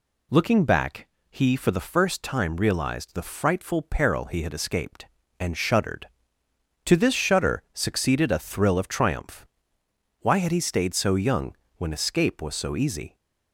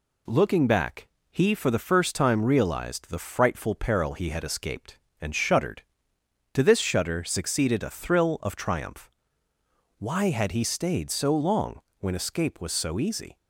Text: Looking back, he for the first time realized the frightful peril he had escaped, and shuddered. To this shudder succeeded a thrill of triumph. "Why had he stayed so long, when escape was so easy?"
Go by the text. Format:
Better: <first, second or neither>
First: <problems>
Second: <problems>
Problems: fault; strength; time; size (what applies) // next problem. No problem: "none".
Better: second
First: says "young" for "long"; at 11.1 s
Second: none